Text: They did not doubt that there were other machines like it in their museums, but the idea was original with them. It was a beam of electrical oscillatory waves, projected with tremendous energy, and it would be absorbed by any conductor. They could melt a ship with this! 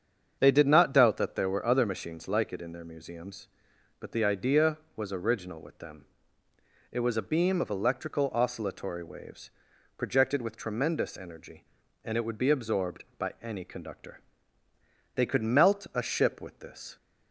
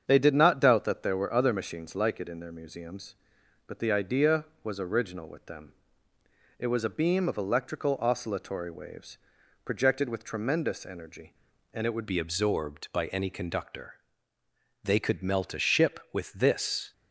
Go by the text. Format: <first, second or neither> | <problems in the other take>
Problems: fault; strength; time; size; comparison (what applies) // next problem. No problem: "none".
first | starts louder than the rest; strong; until 1.1 s; 7.5 dB; strong in the first // changes voice at "be"; from 12.0 s on; 4.9 s long